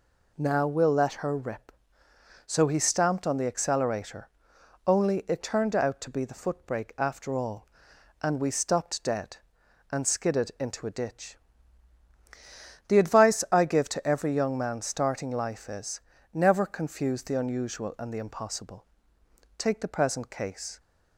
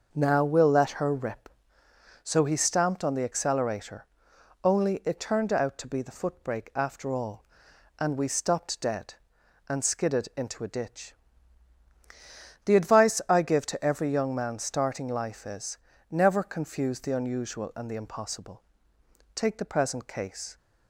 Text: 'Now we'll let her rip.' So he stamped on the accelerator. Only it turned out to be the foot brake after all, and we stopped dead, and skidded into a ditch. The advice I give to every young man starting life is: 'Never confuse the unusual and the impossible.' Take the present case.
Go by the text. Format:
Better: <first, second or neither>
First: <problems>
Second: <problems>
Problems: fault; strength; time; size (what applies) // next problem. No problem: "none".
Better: first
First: none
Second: starts louder than the rest; noticeable; until 1.8 s; 6 dB